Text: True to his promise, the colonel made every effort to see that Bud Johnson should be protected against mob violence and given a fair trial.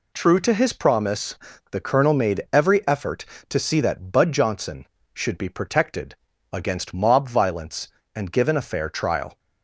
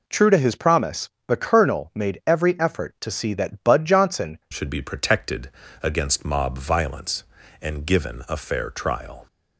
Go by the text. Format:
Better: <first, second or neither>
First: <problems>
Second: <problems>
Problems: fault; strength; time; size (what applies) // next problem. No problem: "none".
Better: first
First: pauses between "protected" and "against"; slight; at 6.1 s; 0.34 s long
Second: changes voice at "should"; from 4.5 s on; 4.7 s long // pauses between "protected" and "against"; slight; at 5.4 s; 0.32 s long